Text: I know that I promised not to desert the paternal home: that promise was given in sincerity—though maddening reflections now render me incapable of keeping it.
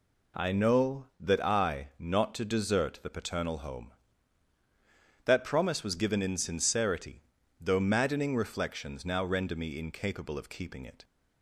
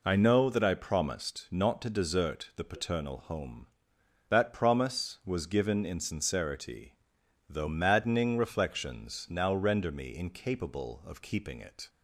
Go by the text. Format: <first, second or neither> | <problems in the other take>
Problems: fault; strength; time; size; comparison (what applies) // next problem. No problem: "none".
second | skips "promised"; at 1.9 s